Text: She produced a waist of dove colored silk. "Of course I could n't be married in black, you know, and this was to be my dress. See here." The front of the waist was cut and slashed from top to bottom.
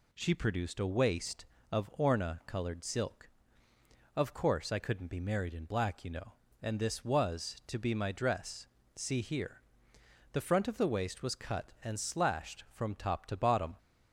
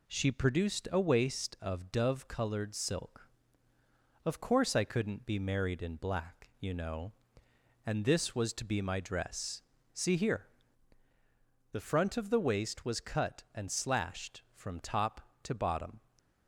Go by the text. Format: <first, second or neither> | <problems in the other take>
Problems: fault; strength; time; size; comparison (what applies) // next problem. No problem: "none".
second | says "orna" for "dove"; at 1.9 s